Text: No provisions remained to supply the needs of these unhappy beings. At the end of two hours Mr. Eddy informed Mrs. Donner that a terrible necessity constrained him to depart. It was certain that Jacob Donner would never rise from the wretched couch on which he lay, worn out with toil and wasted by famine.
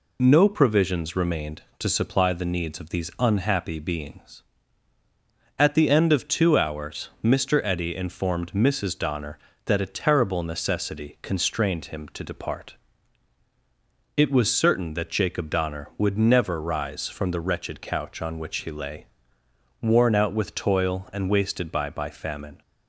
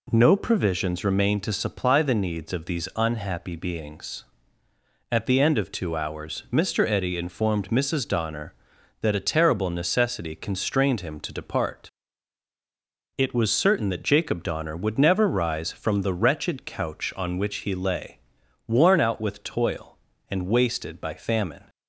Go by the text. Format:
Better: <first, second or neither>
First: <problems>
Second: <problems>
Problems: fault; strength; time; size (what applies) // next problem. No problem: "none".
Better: second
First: says "by" twice; at 21.8 s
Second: none